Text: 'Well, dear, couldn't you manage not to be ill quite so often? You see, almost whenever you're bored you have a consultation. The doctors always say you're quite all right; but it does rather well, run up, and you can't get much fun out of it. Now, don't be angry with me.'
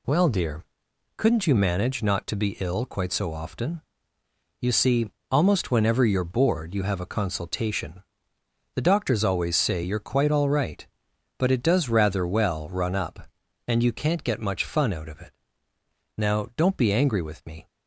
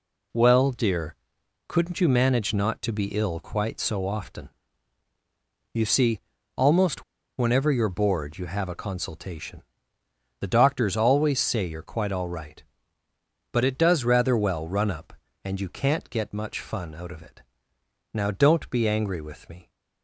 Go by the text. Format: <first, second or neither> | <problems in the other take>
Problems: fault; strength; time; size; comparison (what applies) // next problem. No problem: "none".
first | pauses between "almost" and "whenever"; slight; at 7.0 s; 0.35 s long